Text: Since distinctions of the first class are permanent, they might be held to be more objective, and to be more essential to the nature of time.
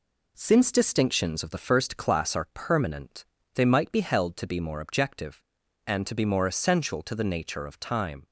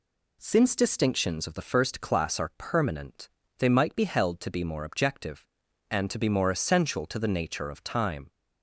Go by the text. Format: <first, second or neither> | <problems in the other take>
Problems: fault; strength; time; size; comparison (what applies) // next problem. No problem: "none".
second | gets quieter; noticeable; throughout; 4.5 dB